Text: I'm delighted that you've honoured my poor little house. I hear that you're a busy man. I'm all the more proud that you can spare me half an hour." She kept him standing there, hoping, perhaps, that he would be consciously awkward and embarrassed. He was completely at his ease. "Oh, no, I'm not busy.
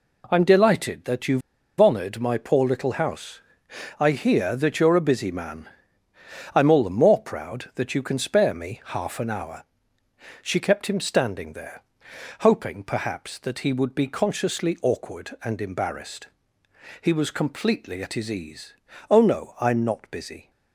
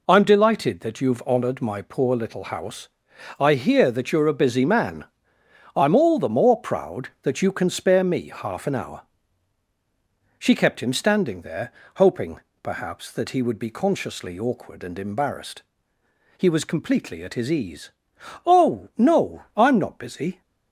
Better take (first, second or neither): second